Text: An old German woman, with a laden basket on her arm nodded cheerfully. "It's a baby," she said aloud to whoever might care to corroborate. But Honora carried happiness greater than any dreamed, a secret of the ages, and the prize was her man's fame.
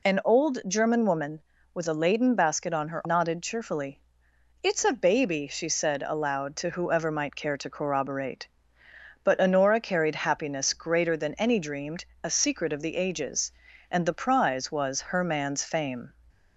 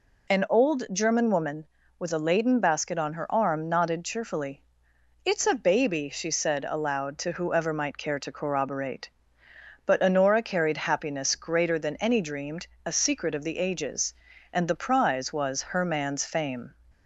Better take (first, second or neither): second